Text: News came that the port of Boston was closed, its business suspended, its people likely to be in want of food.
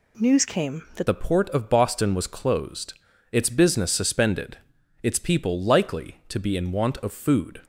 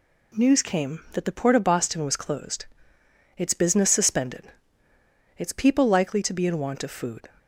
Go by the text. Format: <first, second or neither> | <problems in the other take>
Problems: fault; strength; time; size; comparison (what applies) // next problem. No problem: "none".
second | changes voice at "the"; from 1.0 s on; 6.6 s long